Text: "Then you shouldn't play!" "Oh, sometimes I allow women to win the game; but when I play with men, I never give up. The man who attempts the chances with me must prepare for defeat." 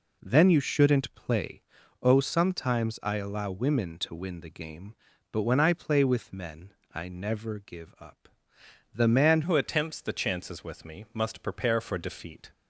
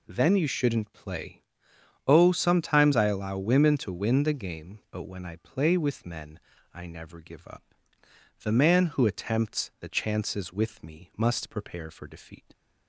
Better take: second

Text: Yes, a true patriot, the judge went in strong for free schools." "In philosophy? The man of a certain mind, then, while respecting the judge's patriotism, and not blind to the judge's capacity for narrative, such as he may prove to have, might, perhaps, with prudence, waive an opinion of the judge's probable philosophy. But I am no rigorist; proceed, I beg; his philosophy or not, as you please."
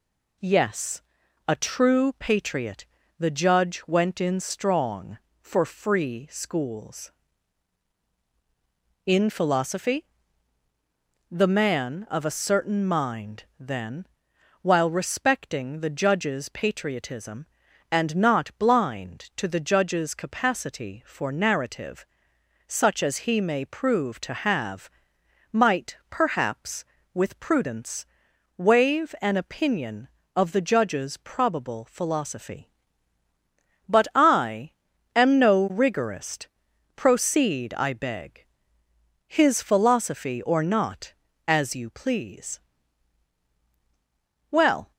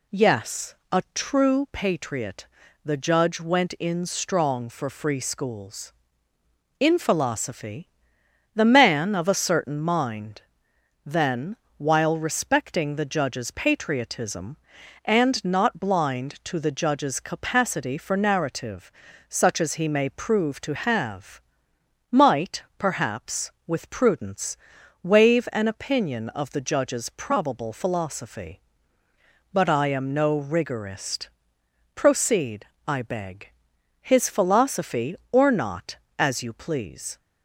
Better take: second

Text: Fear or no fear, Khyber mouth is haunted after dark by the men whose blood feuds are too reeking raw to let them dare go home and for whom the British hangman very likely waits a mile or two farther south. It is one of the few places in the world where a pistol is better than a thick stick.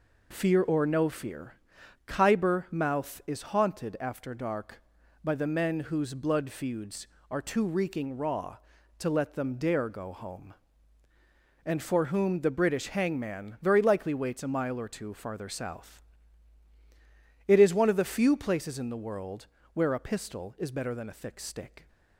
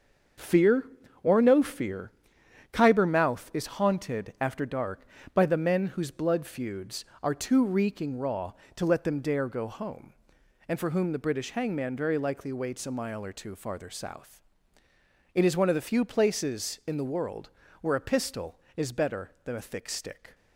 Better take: first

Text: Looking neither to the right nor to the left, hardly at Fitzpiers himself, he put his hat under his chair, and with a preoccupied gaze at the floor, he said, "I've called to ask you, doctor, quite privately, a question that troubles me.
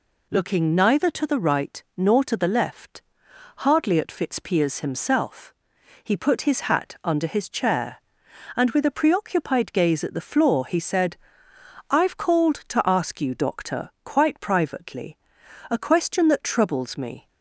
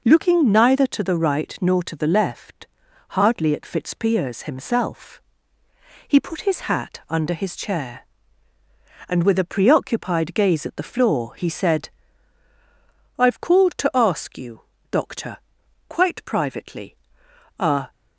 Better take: first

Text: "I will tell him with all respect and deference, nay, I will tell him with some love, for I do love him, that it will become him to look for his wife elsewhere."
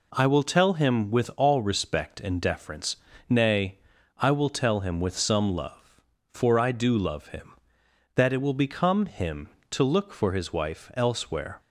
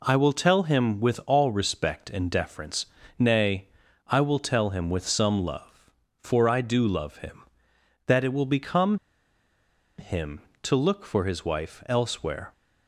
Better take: first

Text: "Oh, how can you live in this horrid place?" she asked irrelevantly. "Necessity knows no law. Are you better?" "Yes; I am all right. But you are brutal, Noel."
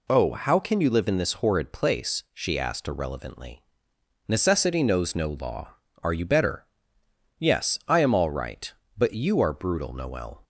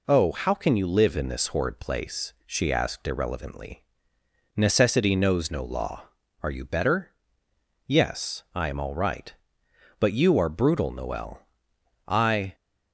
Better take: first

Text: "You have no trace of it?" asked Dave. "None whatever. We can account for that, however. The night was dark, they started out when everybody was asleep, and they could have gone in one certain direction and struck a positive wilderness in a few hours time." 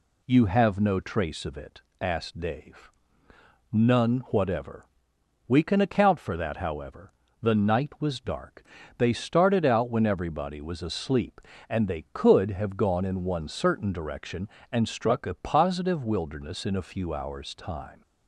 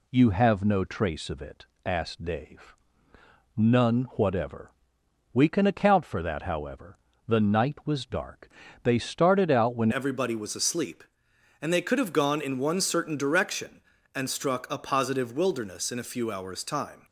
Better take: first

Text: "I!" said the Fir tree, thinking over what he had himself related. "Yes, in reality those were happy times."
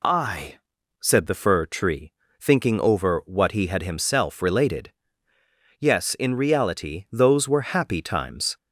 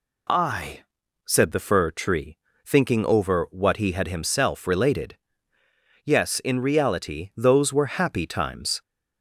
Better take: neither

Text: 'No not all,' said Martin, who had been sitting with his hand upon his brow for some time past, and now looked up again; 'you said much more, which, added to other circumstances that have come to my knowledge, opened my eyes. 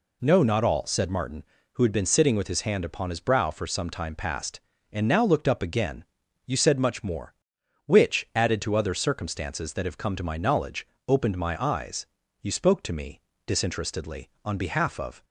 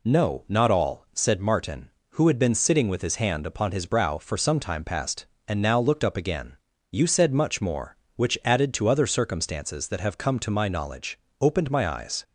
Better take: second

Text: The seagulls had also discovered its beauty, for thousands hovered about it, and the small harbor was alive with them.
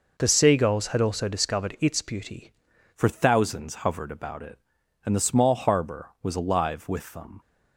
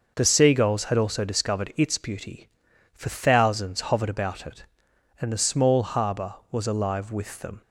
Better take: second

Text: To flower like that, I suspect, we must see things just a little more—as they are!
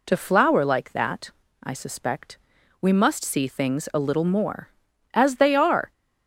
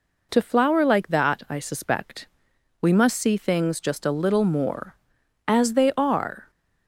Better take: second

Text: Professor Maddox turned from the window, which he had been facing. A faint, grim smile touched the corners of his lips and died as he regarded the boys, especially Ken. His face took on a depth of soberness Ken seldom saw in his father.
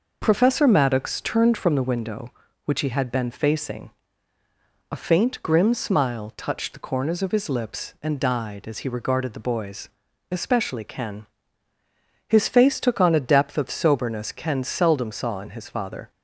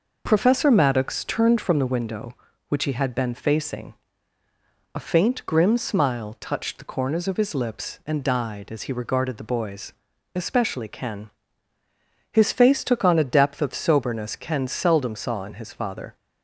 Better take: neither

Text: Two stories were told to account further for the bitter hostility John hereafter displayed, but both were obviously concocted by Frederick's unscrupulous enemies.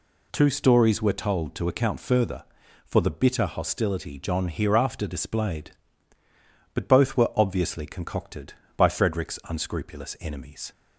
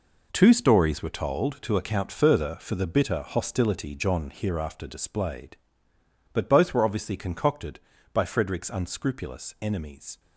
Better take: first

